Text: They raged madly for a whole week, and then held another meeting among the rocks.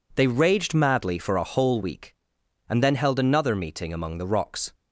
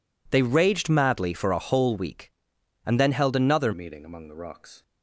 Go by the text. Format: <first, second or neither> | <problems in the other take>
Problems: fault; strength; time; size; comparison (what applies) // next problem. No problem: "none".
first | changes voice at "meeting"; from 3.7 s on; 1.1 s long